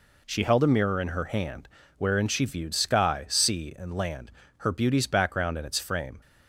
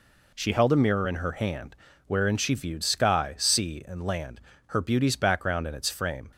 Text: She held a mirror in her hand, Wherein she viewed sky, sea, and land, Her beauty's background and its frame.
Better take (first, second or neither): neither